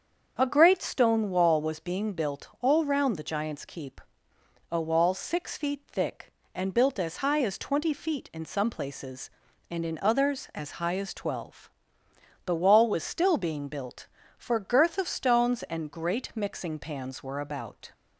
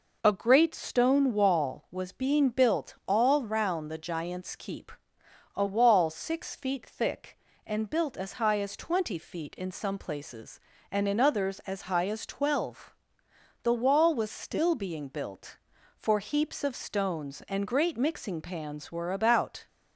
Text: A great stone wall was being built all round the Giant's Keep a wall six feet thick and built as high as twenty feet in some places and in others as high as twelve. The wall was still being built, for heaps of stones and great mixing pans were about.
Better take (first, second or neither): second